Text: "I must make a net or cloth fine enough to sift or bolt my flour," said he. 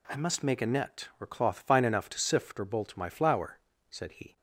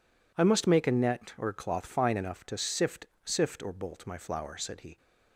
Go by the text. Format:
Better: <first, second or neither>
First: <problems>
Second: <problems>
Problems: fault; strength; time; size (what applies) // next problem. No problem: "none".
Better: first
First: none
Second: says "sift" twice; at 3.2 s